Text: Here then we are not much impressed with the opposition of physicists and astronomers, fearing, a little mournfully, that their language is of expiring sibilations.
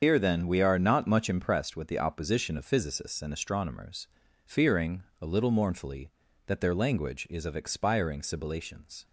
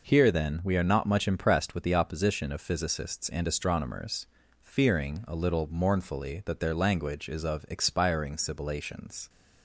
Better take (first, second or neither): second